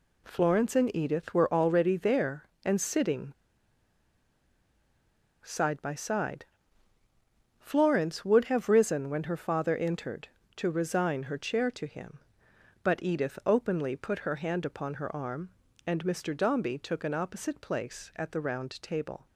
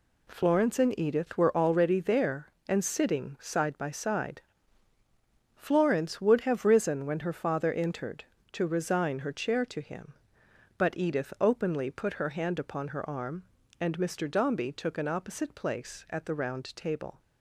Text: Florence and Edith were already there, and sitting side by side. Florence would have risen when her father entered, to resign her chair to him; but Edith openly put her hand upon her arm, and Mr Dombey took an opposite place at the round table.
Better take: second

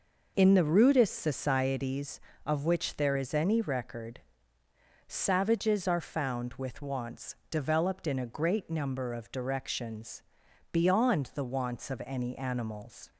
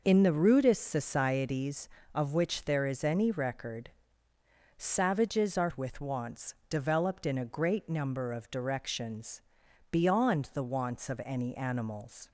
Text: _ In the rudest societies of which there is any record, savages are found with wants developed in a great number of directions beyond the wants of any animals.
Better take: first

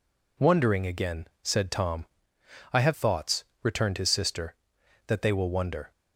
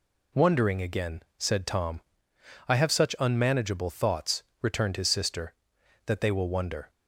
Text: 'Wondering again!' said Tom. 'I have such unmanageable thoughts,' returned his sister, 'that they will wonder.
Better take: second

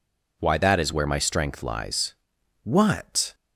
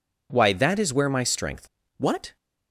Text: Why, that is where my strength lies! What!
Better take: first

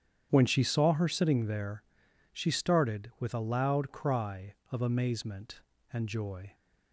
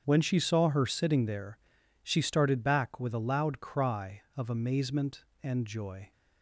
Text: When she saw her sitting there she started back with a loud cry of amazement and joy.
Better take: second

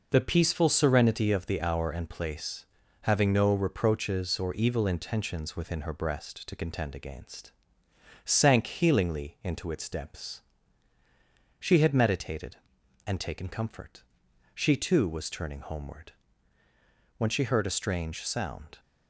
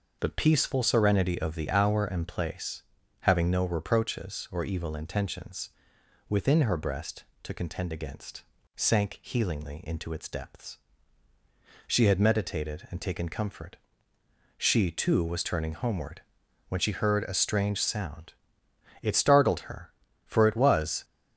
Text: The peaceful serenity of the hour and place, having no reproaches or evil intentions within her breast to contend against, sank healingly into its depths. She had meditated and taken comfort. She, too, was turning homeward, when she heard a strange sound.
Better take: first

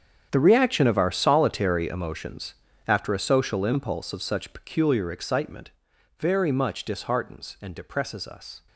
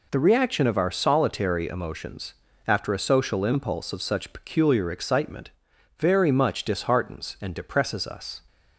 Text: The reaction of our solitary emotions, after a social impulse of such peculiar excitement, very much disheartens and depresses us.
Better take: second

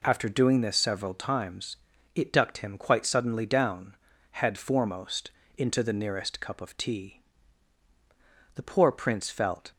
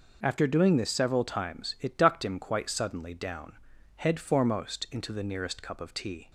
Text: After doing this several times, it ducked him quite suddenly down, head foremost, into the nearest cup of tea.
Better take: second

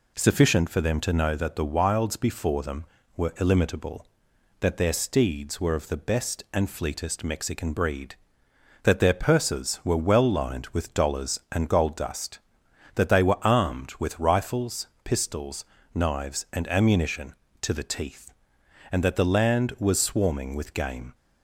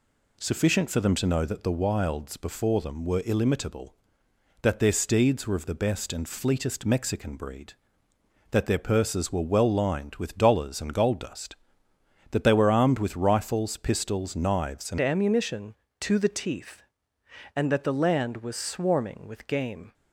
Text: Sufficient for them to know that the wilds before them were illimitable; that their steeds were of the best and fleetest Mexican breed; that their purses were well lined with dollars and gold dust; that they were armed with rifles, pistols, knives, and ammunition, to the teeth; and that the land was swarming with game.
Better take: first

